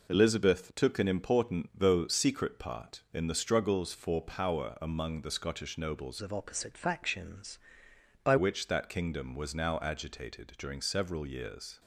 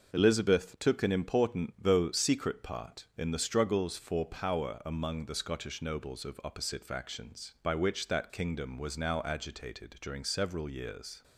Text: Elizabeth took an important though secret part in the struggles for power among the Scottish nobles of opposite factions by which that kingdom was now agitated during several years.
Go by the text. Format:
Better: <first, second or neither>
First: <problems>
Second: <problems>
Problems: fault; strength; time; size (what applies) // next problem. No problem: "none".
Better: second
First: changes voice from "of" to "by"; from 6.2 to 8.3 s; 2.1 s long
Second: none